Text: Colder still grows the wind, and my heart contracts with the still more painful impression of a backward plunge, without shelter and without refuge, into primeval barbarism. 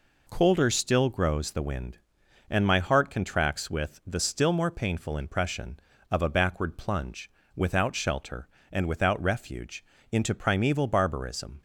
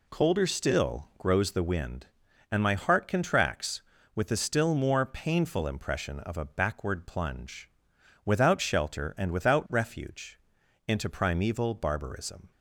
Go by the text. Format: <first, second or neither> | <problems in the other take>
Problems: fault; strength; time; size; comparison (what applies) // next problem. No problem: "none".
neither | none